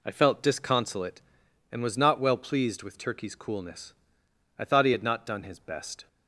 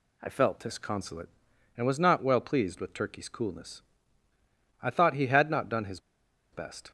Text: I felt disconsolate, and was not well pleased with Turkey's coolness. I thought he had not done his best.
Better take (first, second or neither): first